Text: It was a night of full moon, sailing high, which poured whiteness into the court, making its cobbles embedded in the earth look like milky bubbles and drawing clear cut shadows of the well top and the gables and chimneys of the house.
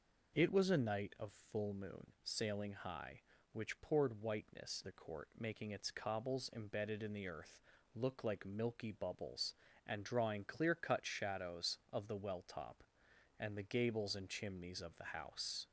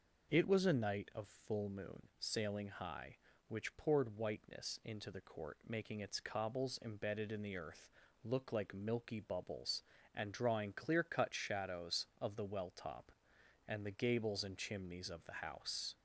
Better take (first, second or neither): second